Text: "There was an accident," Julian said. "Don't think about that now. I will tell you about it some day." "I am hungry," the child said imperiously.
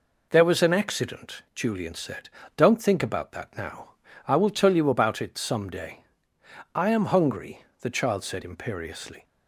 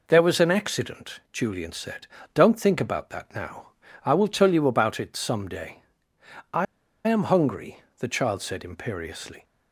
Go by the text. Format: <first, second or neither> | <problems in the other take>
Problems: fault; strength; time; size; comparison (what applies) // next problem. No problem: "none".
first | pauses between "I" and "am"; at 6.6 s; 0.42 s long